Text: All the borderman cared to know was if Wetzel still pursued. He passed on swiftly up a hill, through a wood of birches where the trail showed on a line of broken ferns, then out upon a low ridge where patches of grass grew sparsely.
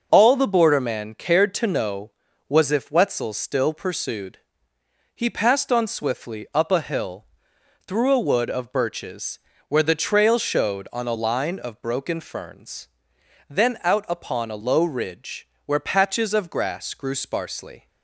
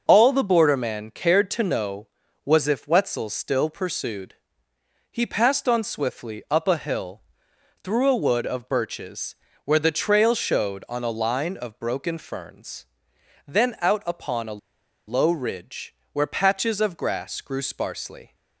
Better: first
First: starts louder than the rest; noticeable; until 1.1 s; 6 dB // pauses between "birches" and "where"; slight; at 9.3 s; 0.30 s long // pauses between "ridge" and "where"; slight; at 15.4 s; 0.20 s long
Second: starts louder than the rest; noticeable; until 1.0 s; 6 dB // pauses between "birches" and "where"; slight; at 9.3 s; 0.30 s long // pauses between "a" and "low"; noticeable; at 14.5 s; 0.48 s long // pauses between "ridge" and "where"; slight; at 15.9 s; 0.20 s long

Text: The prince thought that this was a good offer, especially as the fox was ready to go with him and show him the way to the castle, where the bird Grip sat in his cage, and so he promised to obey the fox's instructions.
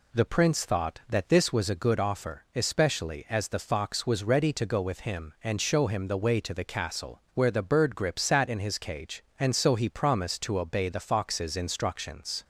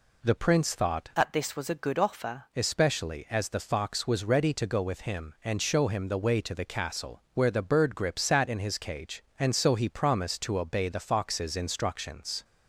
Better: first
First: none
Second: changes voice from "that" to "offer"; from 1.1 to 2.4 s; 1.3 s long

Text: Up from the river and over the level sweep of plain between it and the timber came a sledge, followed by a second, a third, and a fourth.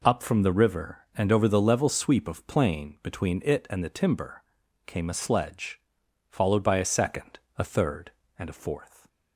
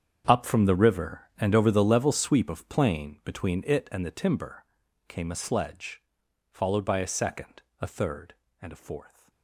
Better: first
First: pauses between "timber" and "came"; at 4.4 s; 0.42 s long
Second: gets quieter; strong; throughout; 17 dB // pauses between "timber" and "came"; at 4.6 s; 0.42 s long

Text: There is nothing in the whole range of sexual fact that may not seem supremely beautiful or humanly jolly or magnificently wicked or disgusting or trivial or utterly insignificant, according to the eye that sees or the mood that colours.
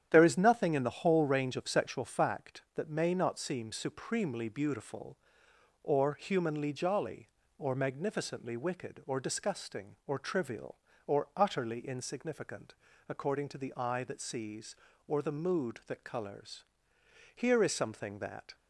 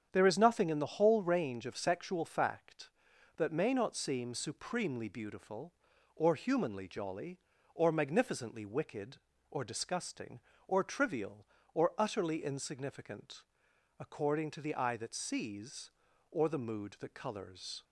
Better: second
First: starts louder than the rest; strong; until 1.1 s; 10 dB // goes on to say "Here is something that"; noticeable; from 17.3 s on; 1.1 s long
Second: starts louder than the rest; strong; until 1.1 s; 8 dB

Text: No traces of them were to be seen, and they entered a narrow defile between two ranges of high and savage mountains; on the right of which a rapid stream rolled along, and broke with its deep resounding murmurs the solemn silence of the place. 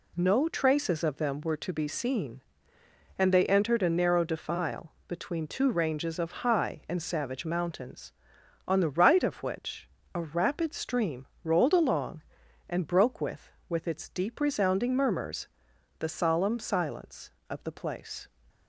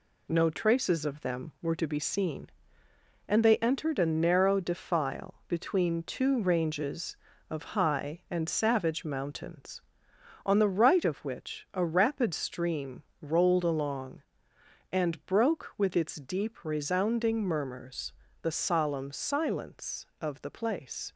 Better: second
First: pauses between "defile" and "between"; slight; at 4.9 s; 0.16 s long // pauses between "which" and "a"; slight; at 9.8 s; 0.26 s long // pauses between "stream" and "rolled"; slight; at 11.2 s; 0.16 s long // says "with" twice; at 13.6 s // pauses between "murmurs" and "the"; noticeable; at 15.4 s; 0.50 s long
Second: pauses between "stream" and "rolled"; slight; at 13.0 s; 0.18 s long // pauses between "murmurs" and "the"; slight; at 18.1 s; 0.30 s long

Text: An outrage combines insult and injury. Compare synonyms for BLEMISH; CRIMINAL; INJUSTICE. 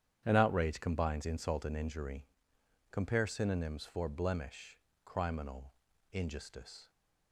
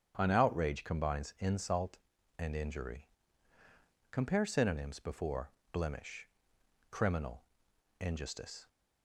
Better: first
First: starts louder than the rest; strong; until 1.2 s; 9.5 dB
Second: starts louder than the rest; strong; until 1.1 s; 9 dB // says "before" for "for"; at 4.9 s

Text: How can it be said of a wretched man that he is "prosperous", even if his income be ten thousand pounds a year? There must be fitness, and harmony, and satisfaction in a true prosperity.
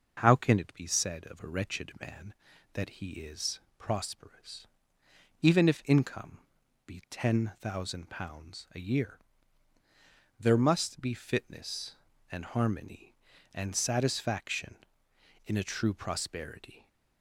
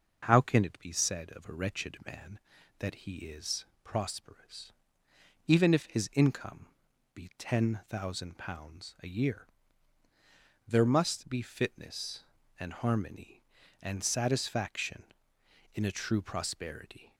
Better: second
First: pauses between "is" and "prosperous"; slight; at 3.6 s; 0.18 s long // skips "his"; at 5.8 s // pauses between "income" and "be"; noticeable; at 6.3 s; 0.46 s long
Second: pauses between "is" and "prosperous"; slight; at 3.6 s; 0.18 s long // pauses between "income" and "be"; noticeable; at 6.6 s; 0.46 s long

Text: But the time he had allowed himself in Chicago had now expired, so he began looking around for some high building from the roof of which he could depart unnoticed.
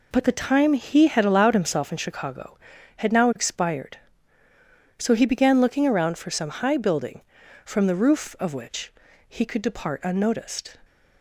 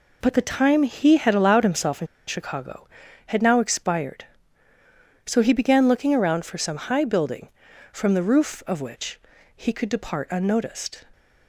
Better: first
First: pauses between "which" and "he"; slight; at 8.9 s; 0.36 s long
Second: pauses between "in" and "Chicago"; slight; at 2.0 s; 0.21 s long // pauses between "which" and "he"; slight; at 9.1 s; 0.36 s long

